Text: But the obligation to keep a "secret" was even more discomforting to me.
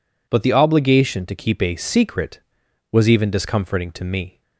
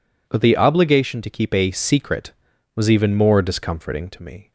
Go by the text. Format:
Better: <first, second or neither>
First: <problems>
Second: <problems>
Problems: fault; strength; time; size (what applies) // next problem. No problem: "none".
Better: second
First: skips "more"; at 3.3 s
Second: none